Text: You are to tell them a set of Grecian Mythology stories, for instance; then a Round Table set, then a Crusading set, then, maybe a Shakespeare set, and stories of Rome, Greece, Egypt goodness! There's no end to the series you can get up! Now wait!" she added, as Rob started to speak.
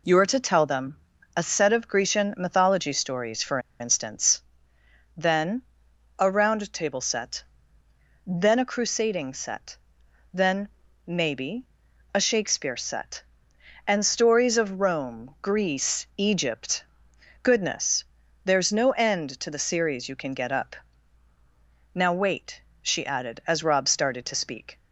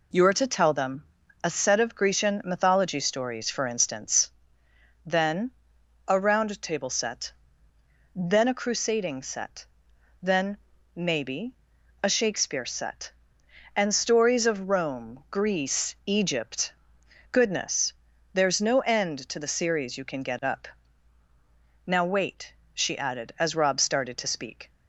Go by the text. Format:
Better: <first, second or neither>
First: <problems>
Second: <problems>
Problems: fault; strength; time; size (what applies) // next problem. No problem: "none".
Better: second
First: pauses between "them" and "a"; slight; at 0.9 s; 0.36 s long // pauses between "for" and "instance"; slight; at 3.5 s; 0.21 s long // pauses between "then" and "a"; noticeable; at 5.6 s; 0.54 s long // pauses between "maybe" and "a"; noticeable; at 11.6 s; 0.48 s long // pauses between "Egypt" and "goodness"; noticeable; at 16.8 s; 0.58 s long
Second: pauses between "them" and "a"; slight; at 1.0 s; 0.36 s long // pauses between "then" and "a"; noticeable; at 5.5 s; 0.54 s long // pauses between "maybe" and "a"; noticeable; at 11.5 s; 0.48 s long // pauses between "Egypt" and "goodness"; noticeable; at 16.7 s; 0.58 s long